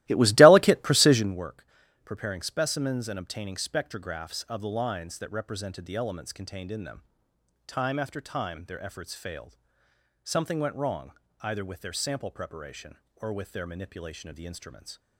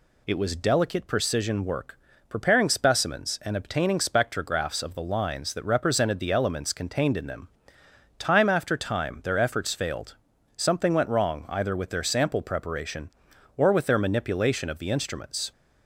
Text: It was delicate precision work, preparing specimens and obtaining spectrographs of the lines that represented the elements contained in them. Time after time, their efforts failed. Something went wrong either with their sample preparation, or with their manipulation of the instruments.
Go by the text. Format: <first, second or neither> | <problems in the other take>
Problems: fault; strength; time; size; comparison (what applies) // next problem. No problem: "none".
second | starts louder than the rest; strong; until 1.4 s; 17 dB // pauses between "wrong" and "either"; slight; at 11.1 s; 0.32 s long